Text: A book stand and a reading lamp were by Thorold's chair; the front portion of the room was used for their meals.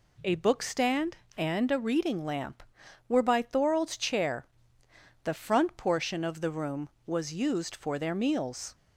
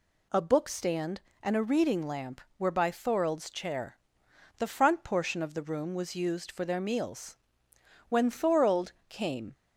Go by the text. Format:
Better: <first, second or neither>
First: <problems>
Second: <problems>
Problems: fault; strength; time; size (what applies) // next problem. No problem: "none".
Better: first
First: none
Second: goes on to say "When Thorold came"; from 8.1 s on; 1.4 s long